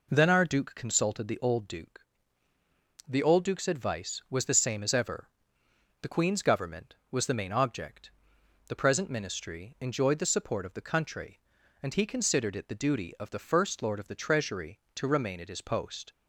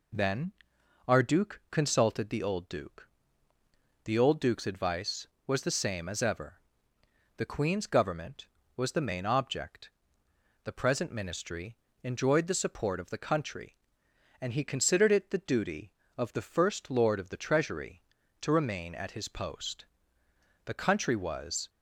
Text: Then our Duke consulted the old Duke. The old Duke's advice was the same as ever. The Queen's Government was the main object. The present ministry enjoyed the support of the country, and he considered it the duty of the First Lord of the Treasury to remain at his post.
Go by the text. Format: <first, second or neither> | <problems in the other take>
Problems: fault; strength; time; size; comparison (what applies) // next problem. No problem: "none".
first | pauses between "Then" and "our"; noticeable; at 0.5 s; 0.56 s long // pauses between "ministry" and "enjoyed"; slight; at 11.7 s; 0.26 s long // goes on to say "The country was"; noticeable; from 20.6 s on; 1.0 s long